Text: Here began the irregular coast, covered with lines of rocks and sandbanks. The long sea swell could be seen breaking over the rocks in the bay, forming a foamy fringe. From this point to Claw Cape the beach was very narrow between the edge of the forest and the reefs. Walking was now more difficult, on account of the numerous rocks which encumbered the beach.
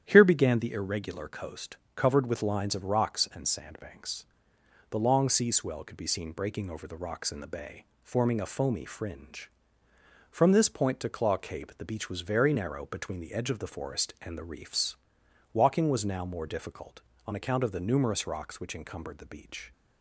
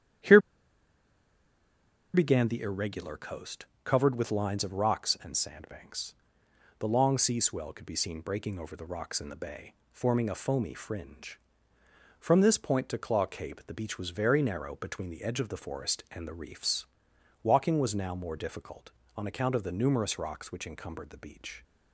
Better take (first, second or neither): first